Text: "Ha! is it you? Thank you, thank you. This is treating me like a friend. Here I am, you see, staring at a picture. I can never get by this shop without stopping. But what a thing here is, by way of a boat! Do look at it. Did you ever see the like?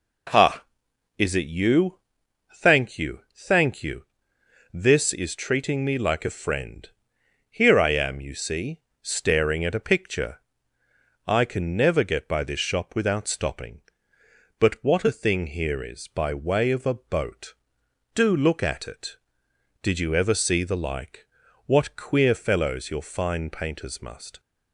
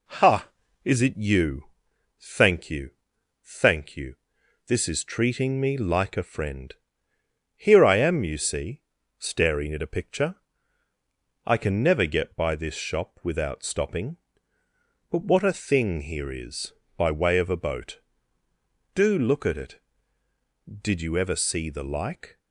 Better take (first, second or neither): second